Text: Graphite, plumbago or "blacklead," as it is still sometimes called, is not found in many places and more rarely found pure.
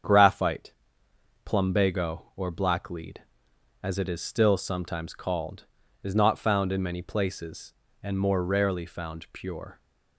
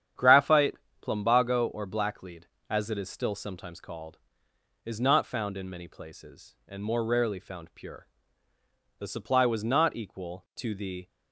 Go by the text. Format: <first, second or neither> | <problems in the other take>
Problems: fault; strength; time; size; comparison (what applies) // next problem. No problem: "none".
first | starts louder than the rest; strong; until 1.4 s; 9 dB; strong in the first // goes on to say "The supply was not equal to the"; strong; from 8.9 s on; 2.1 s long